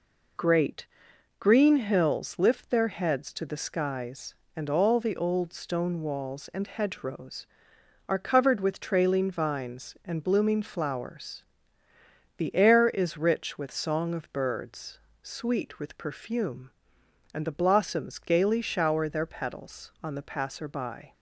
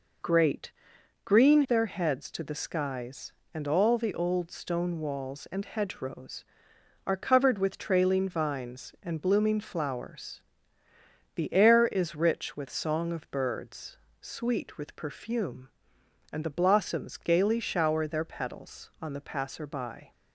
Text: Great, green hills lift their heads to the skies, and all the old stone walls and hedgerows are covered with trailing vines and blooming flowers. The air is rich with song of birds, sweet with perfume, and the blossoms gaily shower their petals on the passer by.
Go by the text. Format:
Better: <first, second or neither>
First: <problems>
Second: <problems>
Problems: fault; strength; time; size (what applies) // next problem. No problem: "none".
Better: first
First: none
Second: skips "hills lift"; at 1.6 s